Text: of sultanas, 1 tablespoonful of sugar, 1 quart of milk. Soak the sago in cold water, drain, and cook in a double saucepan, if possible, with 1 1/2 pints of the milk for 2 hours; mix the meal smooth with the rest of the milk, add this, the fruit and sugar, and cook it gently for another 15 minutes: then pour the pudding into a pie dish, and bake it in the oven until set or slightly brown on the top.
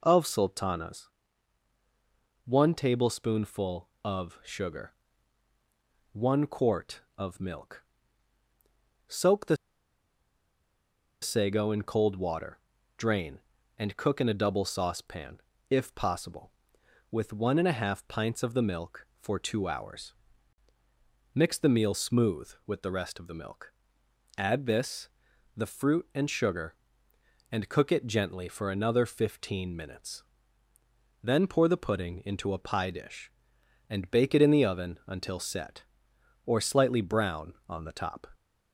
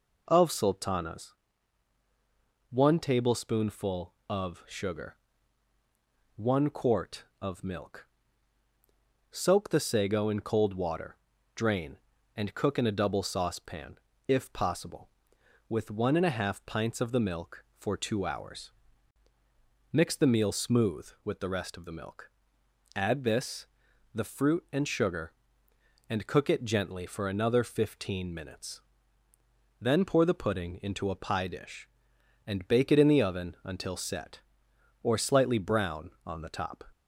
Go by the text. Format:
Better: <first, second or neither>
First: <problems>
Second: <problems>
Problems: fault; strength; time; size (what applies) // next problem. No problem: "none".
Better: second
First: pauses between "the" and "sago"; strong; at 9.5 s; 1.6 s long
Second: none